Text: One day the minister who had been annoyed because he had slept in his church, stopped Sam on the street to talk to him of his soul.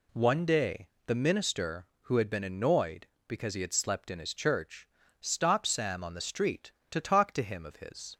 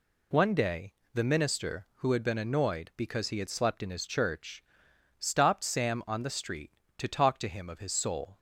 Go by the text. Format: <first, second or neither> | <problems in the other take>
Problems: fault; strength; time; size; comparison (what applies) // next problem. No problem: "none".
second | pauses between "day" and "the"; slight; at 0.8 s; 0.18 s long; slight in the second // stops before "soul"; at 8.1 s